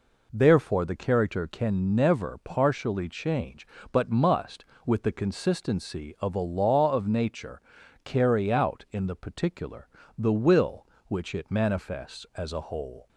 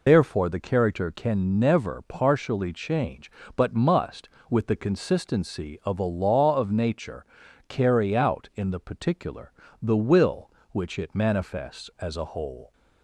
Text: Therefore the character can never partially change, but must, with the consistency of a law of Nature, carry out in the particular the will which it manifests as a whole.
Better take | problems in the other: first | loses the start of "Therefore"; at 0.0 s; 125 ms // pauses between "particular" and "the"; slight; at 9.5 s; 0.28 s long; slight in the first

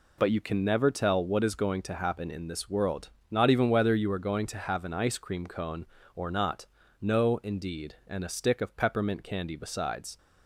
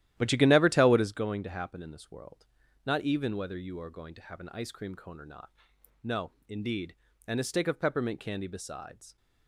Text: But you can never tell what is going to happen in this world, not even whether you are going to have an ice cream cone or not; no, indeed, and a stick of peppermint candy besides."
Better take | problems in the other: first | starts louder than the rest; strong; until 1.3 s; 13 dB

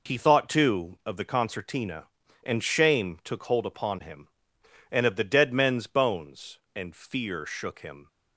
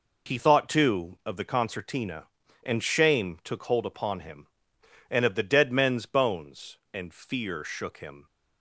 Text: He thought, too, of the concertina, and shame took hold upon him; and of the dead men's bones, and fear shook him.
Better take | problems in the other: neither | none

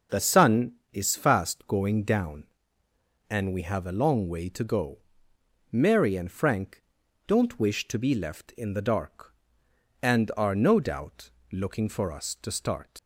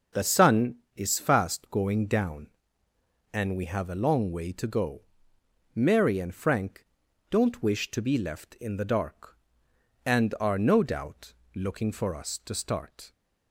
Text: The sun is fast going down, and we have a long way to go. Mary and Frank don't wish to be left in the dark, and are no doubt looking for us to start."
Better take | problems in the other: second | starts louder than the rest; until 1.3 s; 6.5 dB; also in the second // pauses between "Frank" and "don't"; noticeable; at 6.8 s; 0.46 s long; noticeable in the second // pauses between "doubt" and "looking"; slight; at 11.2 s; 0.22 s long; slight in the second // leaves "start" unfinished; at 12.9 s; 105 ms

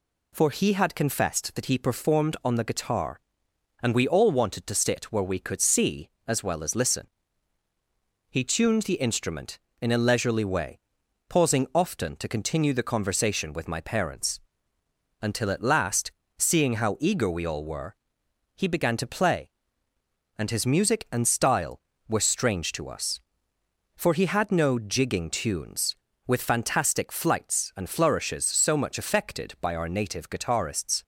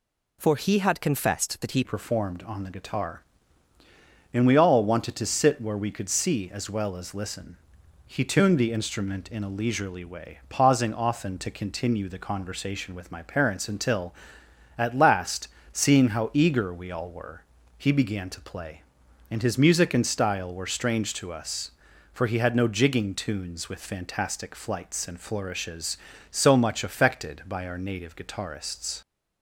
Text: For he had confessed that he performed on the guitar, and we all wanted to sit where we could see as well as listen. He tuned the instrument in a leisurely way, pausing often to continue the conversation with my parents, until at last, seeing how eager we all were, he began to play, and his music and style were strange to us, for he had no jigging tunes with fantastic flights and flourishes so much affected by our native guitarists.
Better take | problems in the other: first | changes voice at "performed"; from 1.8 s on; 27.2 s long

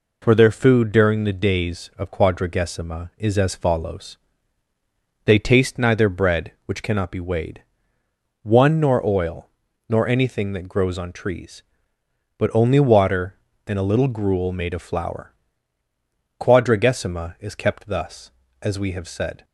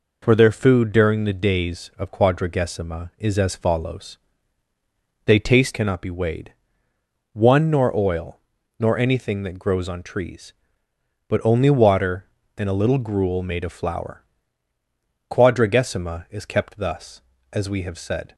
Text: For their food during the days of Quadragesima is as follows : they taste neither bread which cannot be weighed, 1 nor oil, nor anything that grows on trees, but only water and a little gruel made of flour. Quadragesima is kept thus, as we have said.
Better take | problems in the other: first | skips "neither bread which"; at 5.7 s

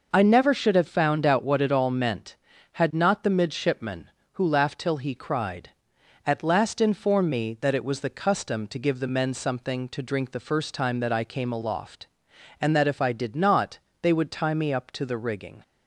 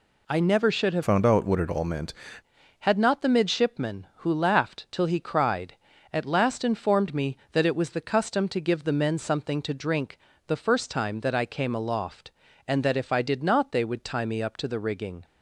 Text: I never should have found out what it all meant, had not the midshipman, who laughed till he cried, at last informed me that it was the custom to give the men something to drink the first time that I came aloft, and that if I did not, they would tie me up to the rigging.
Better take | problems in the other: first | changes voice from "found" to "meant"; from 1.0 to 2.1 s; 1.1 s long // pauses between "drink" and "the"; slight; at 10.1 s; 0.30 s long

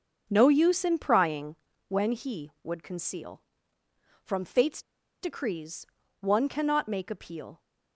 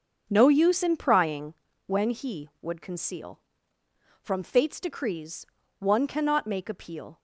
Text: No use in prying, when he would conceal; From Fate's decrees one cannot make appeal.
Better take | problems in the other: second | starts louder than the rest; noticeable; until 1.3 s; 6 dB; also in the second // pauses between "Fate's" and "decrees"; at 4.8 s; 0.40 s long // pauses between "decrees" and "one"; slight; at 5.8 s; 0.36 s long; slight in the second

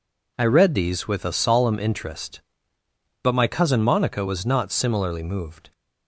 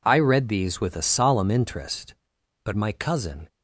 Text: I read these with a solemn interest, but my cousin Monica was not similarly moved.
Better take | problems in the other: first | stops before "Monica was not similarly moved"; at 3.4 s

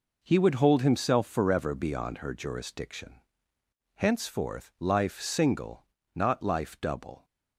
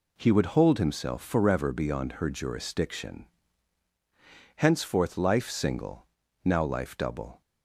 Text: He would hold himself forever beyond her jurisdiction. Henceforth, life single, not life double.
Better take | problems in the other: first | says "now" for "not"; at 6.4 s

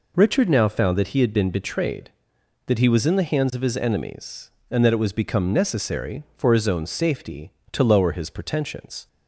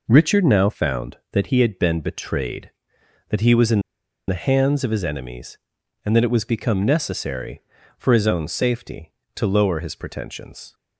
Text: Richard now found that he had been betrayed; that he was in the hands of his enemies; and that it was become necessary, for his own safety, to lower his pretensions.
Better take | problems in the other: first | pauses between "in" and "the"; noticeable; at 3.7 s; 0.48 s long

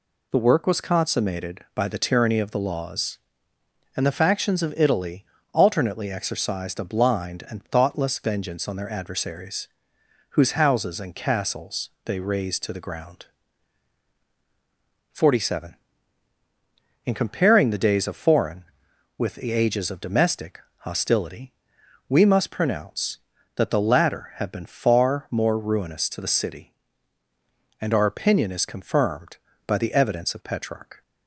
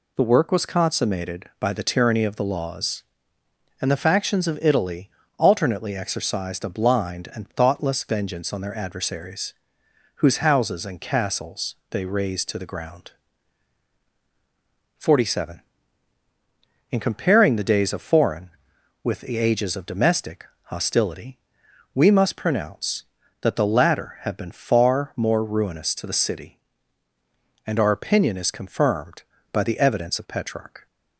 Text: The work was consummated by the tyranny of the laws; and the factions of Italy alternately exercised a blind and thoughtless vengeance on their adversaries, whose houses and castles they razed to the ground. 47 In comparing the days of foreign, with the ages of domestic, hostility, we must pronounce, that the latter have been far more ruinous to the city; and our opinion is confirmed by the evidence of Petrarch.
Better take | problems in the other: neither | pauses between "Italy" and "alternately"; slight; the same in both // pauses between "castles" and "they"; slight; the same in both

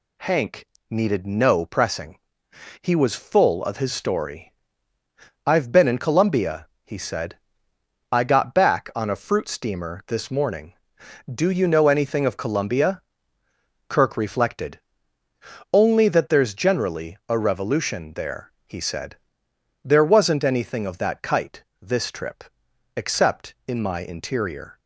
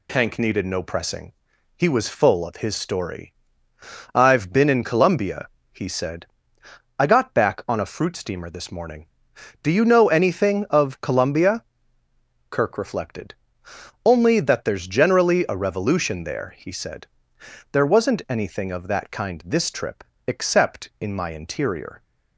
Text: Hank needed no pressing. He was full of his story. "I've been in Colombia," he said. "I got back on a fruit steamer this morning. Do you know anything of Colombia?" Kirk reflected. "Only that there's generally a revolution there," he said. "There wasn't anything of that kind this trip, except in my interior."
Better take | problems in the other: second | pauses between "Hank" and "needed"; slight; at 0.6 s; 0.24 s long // says "kite" for "kind"; at 21.2 s

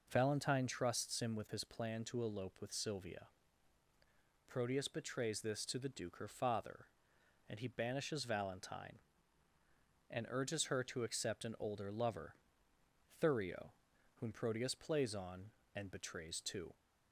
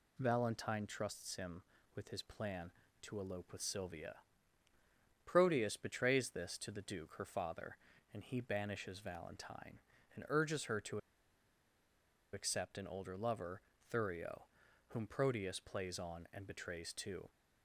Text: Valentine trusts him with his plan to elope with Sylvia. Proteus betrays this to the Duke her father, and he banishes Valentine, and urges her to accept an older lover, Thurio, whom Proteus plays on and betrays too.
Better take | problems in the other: first | pauses between "to" and "accept"; strong; at 10.9 s; 1.3 s long

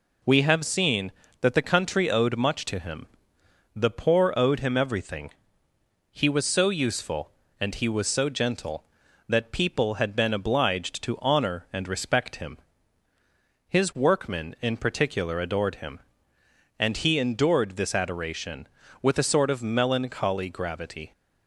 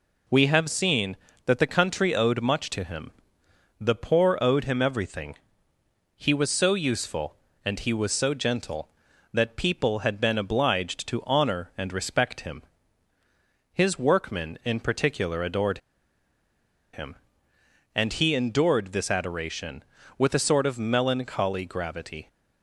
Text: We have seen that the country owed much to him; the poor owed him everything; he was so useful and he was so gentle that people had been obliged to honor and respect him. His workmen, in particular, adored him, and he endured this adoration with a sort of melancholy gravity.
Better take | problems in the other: first | pauses between "adored" and "him"; at 15.7 s; 1.1 s long

